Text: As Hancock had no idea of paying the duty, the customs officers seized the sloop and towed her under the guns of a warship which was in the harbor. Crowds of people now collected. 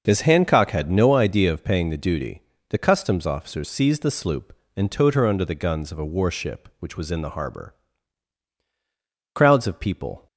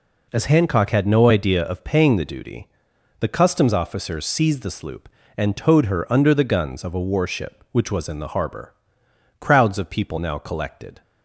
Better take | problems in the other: second | starts louder than the rest; noticeable; until 1.0 s; 6 dB // stops before "now collected"; at 10.2 s

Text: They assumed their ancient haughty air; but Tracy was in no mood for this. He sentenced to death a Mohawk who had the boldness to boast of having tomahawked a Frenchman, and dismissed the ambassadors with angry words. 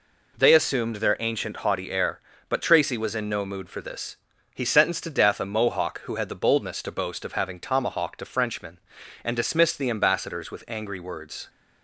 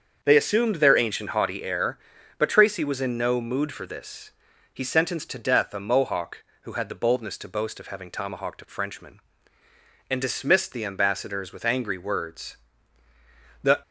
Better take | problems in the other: first | starts louder than the rest; until 1.2 s; 7 dB // goes on to say "The"; slight; from 13.6 s on; 0.18 s long

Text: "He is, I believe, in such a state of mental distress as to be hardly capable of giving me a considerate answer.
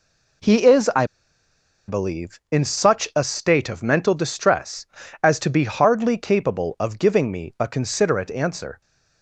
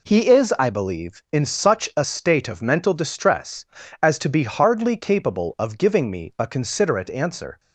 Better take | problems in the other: second | pauses between "I" and "believe"; noticeable; at 1.0 s; 0.82 s long

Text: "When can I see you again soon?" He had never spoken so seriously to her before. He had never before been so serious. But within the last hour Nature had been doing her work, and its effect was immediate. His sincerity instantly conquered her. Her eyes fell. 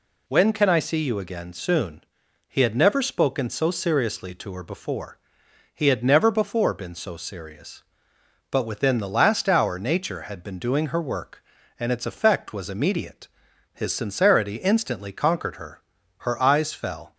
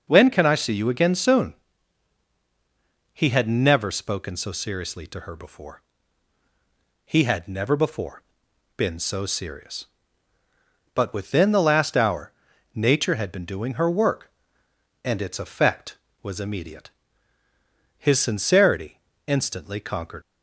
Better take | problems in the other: first | pauses between "before" and "been"; noticeable; at 8.2 s; 0.56 s long // pauses between "hour" and "Nature"; at 12.3 s; 0.42 s long // pauses between "sincerity" and "instantly"; slight; at 19.0 s; 0.26 s long // stops before "her Her eyes fell"; at 20.2 s

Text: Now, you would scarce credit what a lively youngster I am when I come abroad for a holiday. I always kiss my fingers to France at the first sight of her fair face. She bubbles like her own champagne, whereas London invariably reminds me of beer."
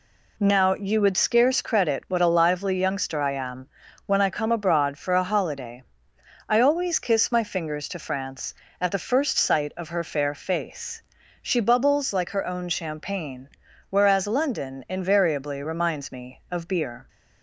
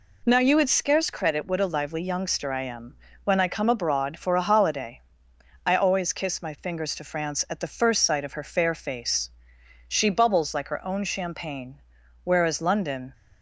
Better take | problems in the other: first | pauses between "am" and "when"; slight; at 2.9 s; 0.28 s long; also in the first // stops before "invariably reminds me of beer"; at 13.1 s

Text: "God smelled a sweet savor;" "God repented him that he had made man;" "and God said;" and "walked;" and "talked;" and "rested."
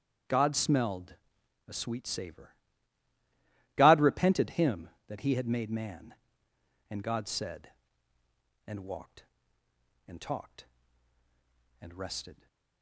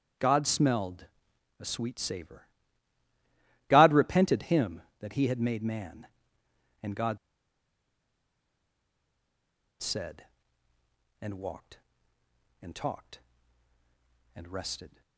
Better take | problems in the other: first | starts louder than the rest; strong; until 1.7 s; 8.5 dB; strong in the first // pauses between "smelled" and "a"; noticeable; at 1.0 s; 0.54 s long; noticeable in the first // pauses between "God" and "said"; strong; at 7.1 s; 2.6 s long

